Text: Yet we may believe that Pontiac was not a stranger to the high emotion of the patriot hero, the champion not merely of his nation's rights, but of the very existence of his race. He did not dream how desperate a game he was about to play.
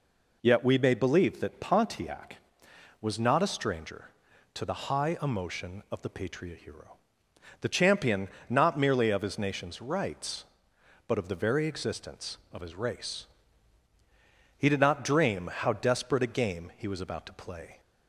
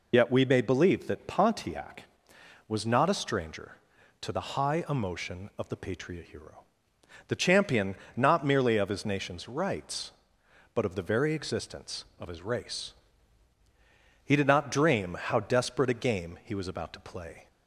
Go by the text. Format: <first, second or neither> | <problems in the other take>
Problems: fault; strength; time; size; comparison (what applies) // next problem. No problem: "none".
first | loses the start of "Yet"; at 0.1 s; 45 ms // pauses between "champion" and "not"; slight; at 7.9 s; 0.20 s long; slight in the first